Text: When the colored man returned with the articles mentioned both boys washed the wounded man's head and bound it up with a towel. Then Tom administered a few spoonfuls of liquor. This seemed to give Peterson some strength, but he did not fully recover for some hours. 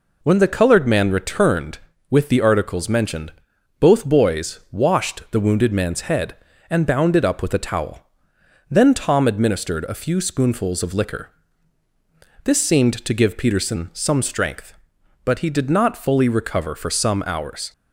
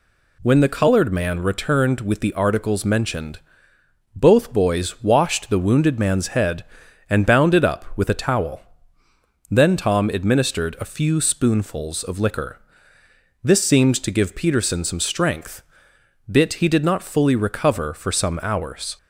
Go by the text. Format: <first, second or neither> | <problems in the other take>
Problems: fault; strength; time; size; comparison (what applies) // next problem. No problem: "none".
first | pauses between "mentioned" and "both"; noticeable; at 3.3 s; 0.76 s long; noticeable in the first // says "bit" for "but"; at 16.2 s